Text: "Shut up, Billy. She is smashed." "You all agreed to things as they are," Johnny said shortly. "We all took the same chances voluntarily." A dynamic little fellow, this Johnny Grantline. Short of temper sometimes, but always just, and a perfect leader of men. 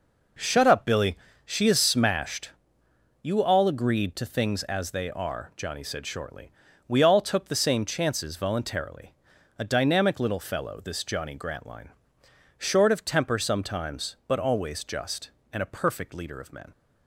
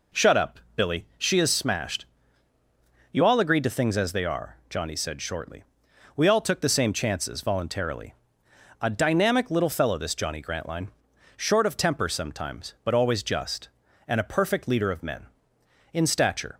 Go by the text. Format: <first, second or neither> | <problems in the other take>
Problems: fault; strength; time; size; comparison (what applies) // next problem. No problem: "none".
first | goes on to say "In stature"; noticeable; from 15.9 s on; 0.64 s long